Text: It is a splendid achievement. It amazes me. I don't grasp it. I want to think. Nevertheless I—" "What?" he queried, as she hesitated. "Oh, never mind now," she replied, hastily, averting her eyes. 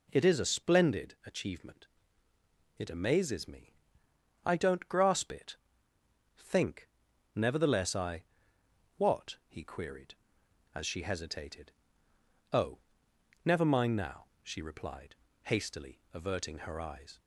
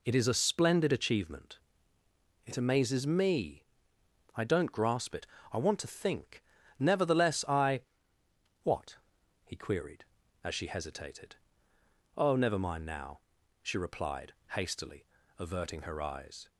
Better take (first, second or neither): second